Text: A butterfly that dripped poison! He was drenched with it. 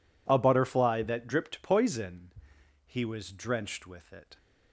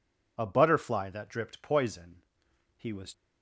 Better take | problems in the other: first | stops before "drenched with it"; at 3.1 s

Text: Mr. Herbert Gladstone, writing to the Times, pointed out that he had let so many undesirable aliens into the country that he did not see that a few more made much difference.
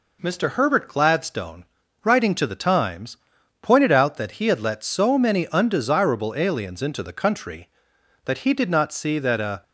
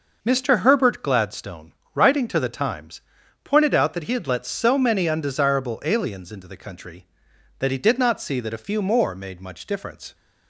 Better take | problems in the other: second | stops before "few more made much difference"; at 9.6 s

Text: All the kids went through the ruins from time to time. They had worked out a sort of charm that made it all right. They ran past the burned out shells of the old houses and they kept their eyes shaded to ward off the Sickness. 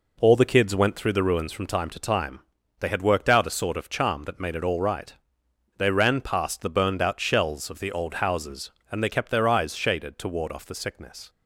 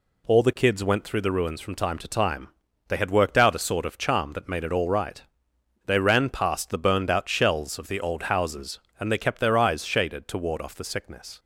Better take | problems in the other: second | starts louder than the rest; noticeable; until 1.8 s; 4 dB

